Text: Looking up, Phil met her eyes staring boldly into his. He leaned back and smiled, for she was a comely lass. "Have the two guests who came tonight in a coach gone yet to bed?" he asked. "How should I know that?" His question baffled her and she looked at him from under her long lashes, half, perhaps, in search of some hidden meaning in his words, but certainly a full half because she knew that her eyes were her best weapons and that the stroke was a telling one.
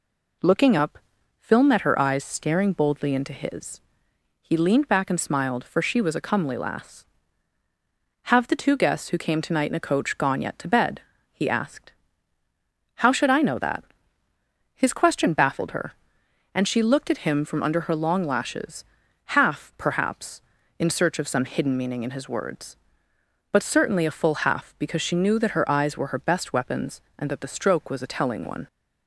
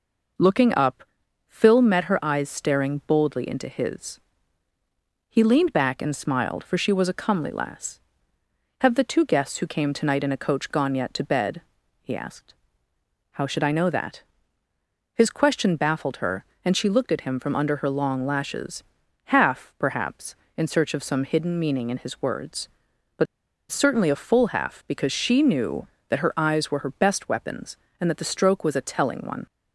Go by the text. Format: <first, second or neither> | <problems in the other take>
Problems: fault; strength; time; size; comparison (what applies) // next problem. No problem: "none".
first | pauses between "but" and "certainly"; noticeable; at 23.2 s; 0.46 s long